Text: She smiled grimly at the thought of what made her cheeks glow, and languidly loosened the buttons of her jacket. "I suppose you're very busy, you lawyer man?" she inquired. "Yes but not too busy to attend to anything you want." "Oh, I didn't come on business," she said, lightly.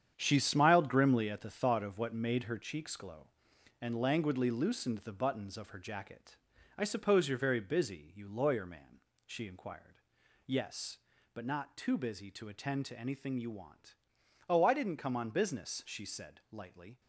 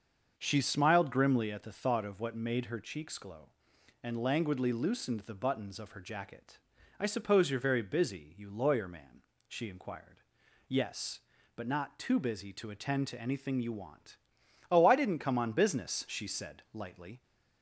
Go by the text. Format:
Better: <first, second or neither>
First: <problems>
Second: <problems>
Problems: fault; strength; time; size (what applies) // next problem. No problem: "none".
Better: second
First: gets quieter; strong; throughout; 10 dB // starts louder than the rest; strong; until 1.1 s; 8.5 dB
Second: starts louder than the rest; until 1.3 s; 6.5 dB